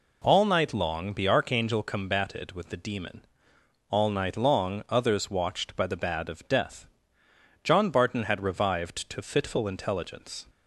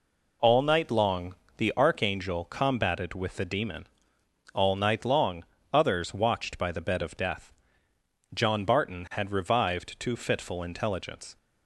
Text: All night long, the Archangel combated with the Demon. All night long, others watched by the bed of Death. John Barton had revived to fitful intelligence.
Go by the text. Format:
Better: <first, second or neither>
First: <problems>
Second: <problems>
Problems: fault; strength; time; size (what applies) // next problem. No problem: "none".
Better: second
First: says "bad" for "bed"; at 5.9 s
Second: none